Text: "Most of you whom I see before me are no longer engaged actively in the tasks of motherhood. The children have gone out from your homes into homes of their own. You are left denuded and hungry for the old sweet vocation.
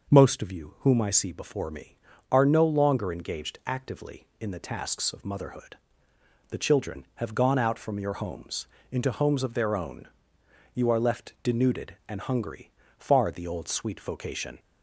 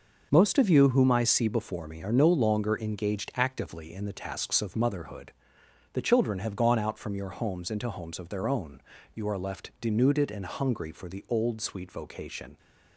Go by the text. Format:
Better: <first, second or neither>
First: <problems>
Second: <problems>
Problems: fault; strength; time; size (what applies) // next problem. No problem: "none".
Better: second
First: pauses between "homes" and "into"; slight; at 8.6 s; 0.22 s long // says "far" for "for"; at 12.9 s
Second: none